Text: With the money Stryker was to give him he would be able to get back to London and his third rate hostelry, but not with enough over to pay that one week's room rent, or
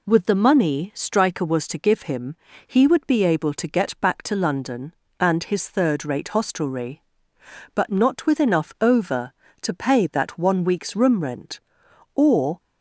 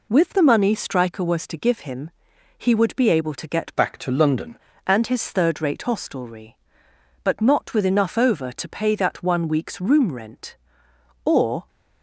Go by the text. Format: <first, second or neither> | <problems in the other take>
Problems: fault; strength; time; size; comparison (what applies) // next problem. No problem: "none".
first | pauses between "him" and "he"; noticeable; at 2.1 s; 0.48 s long; slight in the first // changes voice from "back" to "London"; from 3.7 to 4.5 s; 0.8 s long